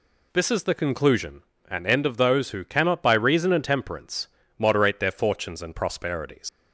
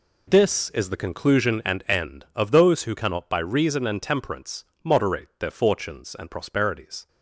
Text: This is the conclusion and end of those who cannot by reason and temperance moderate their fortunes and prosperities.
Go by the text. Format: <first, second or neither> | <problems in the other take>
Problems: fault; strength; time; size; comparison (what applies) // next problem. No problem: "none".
second | pauses between "temperance" and "moderate"; slight; at 4.2 s; 0.32 s long; slight in the second // leaves "prosperities" unfinished; at 6.4 s; 95 ms